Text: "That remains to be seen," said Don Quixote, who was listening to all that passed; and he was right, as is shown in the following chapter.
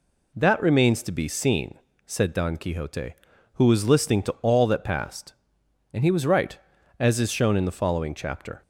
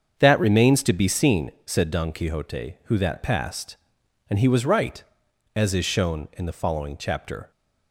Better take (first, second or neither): first